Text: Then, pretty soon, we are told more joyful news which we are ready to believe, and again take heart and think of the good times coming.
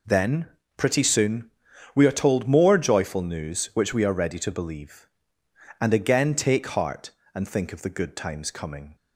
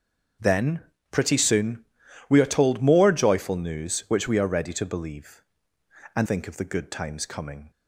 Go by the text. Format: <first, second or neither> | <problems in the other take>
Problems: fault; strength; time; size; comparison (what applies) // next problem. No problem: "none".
first | starts louder than the rest; strong; until 1.7 s; 7 dB // skips "again take heart and"; at 6.2 s